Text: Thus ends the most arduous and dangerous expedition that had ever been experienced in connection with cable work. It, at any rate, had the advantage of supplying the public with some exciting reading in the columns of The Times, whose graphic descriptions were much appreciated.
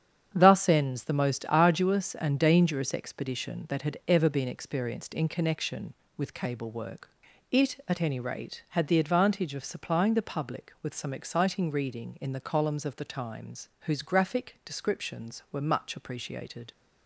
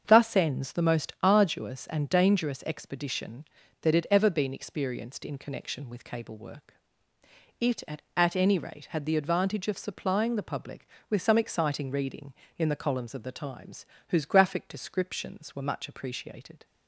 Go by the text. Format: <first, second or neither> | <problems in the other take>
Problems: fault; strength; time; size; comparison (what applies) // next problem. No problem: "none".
first | starts louder than the rest; strong; until 1.0 s; 7 dB; strong in the first // says "at" twice; at 8.1 s